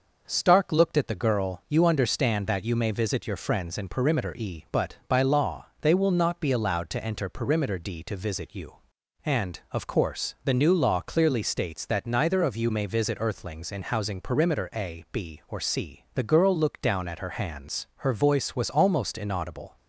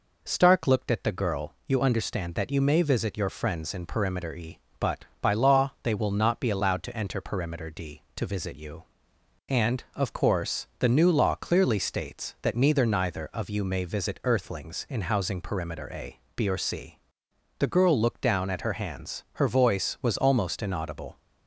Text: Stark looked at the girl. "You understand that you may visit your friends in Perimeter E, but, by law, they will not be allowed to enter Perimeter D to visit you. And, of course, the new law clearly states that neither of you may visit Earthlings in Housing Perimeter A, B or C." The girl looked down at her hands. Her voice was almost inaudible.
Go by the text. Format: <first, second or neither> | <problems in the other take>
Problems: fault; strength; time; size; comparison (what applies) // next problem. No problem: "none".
first | says "neither" twice; at 12.8 s